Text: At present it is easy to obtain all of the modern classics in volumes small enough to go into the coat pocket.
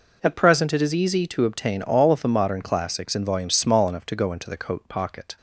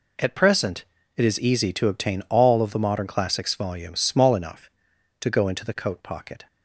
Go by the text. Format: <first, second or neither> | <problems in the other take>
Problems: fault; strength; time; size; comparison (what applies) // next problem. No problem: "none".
first | pauses between "present" and "it"; slight; at 0.8 s; 0.32 s long // skips "in"; at 3.5 s